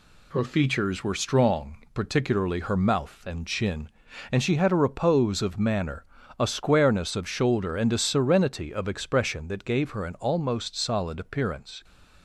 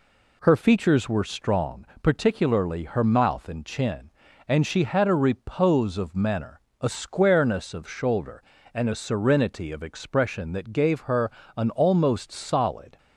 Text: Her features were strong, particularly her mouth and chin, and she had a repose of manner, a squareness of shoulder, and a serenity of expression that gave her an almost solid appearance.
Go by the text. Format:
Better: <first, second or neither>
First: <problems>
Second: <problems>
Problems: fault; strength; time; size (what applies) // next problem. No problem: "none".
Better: first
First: none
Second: pauses between "her" and "an"; slight; at 11.3 s; 0.24 s long // stops before "appearance"; at 12.9 s